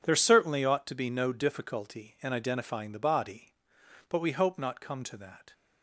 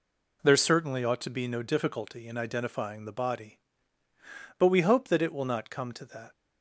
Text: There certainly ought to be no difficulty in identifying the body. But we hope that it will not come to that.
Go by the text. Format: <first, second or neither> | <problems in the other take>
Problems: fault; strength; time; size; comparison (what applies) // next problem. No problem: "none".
second | skips "that it will"; at 4.5 s